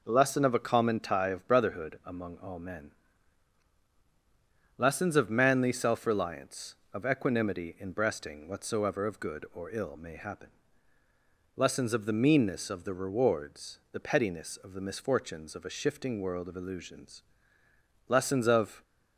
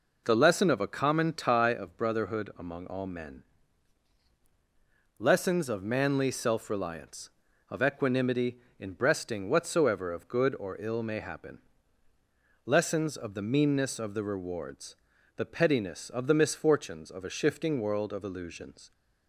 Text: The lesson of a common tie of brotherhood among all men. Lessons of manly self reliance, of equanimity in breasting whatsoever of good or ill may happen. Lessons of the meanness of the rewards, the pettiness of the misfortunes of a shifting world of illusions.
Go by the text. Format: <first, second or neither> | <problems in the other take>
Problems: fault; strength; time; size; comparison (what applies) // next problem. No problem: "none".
second | goes on to say "Lessons of"; noticeable; from 18.0 s on; 0.74 s long